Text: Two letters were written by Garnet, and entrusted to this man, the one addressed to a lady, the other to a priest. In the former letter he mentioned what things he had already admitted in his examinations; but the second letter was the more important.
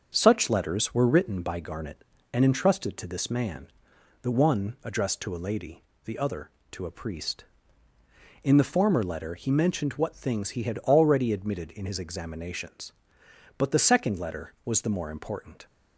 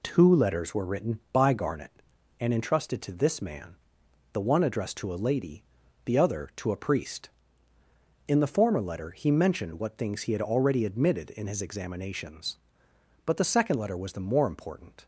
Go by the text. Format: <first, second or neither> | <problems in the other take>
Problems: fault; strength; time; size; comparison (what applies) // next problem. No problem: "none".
second | starts louder than the rest; until 1.1 s; 6.5 dB // says "Such" for "Two"; at 0.1 s